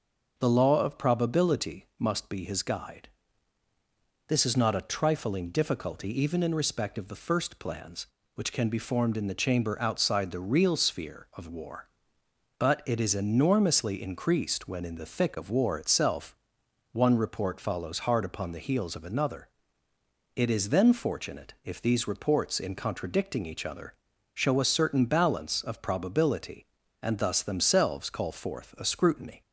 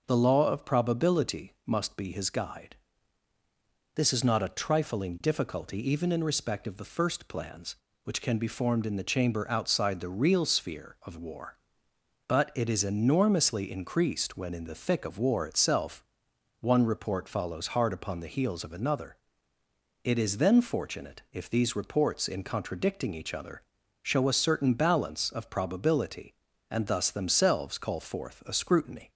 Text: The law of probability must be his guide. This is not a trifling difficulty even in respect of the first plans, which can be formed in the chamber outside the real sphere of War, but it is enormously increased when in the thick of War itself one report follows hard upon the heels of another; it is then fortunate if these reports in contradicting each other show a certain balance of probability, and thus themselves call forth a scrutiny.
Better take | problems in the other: neither | pauses between "itself" and "one"; noticeable; the same in both // pauses between "other" and "show"; the same in both

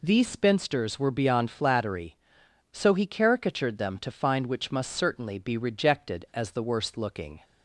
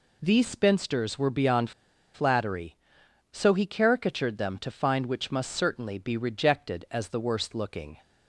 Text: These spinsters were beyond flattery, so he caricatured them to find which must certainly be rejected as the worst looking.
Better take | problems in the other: first | pauses between "beyond" and "flattery"; at 1.7 s; 0.43 s long

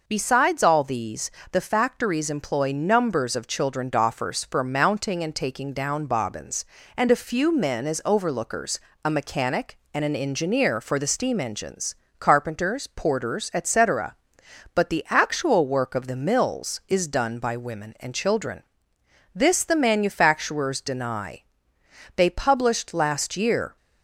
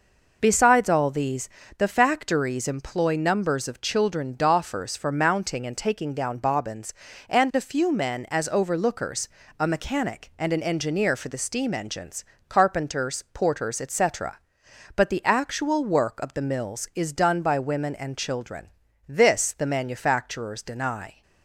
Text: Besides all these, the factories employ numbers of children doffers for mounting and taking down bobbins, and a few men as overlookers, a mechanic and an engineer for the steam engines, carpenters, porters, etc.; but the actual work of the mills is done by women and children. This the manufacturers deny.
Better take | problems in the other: second | goes on to say "They published last year"; from 22.1 s on; 1.6 s long

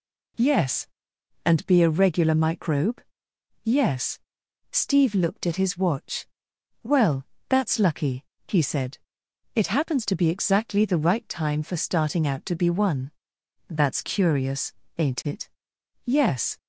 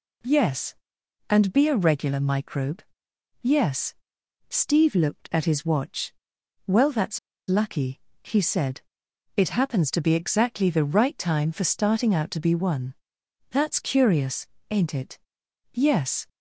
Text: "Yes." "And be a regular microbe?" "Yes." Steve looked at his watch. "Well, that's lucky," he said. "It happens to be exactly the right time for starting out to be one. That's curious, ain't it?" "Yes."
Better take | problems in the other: first | pauses between "that's" and "lucky"; slight; at 7.1 s; 0.30 s long

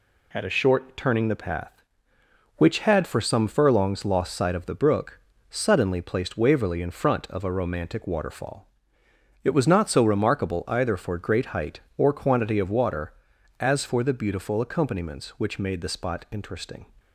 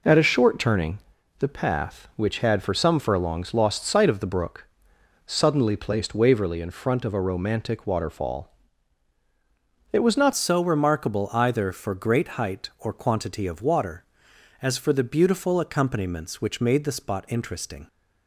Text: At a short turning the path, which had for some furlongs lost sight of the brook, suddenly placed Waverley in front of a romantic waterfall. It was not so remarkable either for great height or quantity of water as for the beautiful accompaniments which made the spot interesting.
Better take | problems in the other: first | pauses between "turning" and "the"; at 0.9 s; 0.40 s long // changes voice at "so"; from 10.3 s on; 7.5 s long

